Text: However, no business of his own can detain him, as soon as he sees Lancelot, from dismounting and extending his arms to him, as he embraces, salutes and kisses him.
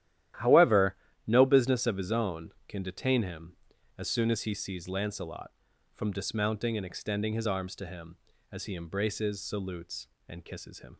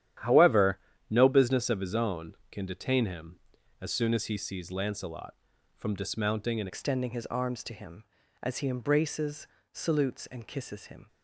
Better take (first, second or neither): first